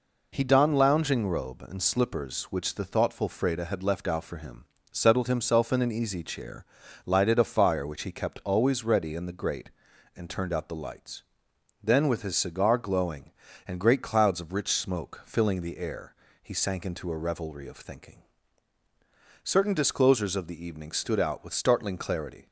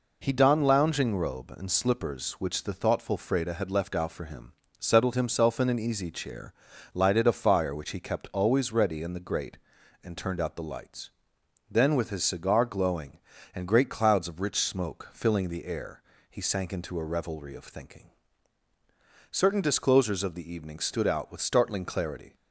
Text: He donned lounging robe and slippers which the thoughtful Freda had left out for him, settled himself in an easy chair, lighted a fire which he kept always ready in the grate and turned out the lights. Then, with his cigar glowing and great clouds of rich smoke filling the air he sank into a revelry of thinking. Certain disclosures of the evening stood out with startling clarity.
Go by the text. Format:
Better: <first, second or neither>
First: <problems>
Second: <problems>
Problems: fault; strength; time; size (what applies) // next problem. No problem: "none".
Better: neither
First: pauses between "air" and "he"; slight; at 16.1 s; 0.26 s long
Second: pauses between "air" and "he"; slight; at 16.0 s; 0.26 s long